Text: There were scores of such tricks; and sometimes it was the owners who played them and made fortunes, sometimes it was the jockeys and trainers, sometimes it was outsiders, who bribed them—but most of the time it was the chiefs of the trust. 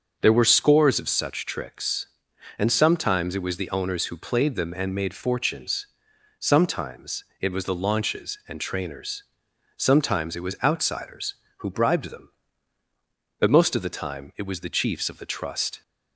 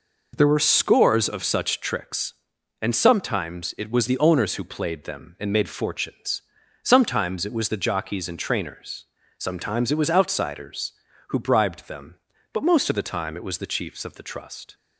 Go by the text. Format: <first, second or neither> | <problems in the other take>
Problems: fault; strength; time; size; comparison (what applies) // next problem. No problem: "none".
second | starts louder than the rest; until 1.2 s; 6.5 dB // pauses between "sometimes" and "it"; slight; at 7.2 s; 0.18 s long // says "launches" for "jockeys"; at 7.7 s